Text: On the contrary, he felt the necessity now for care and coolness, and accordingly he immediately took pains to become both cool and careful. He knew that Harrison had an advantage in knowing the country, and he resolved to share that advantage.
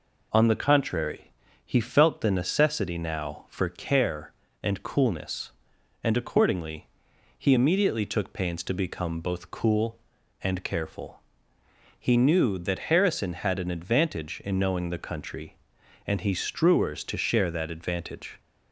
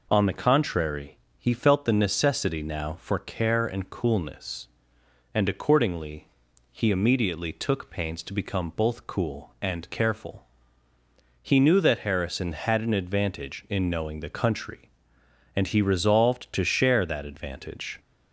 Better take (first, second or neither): second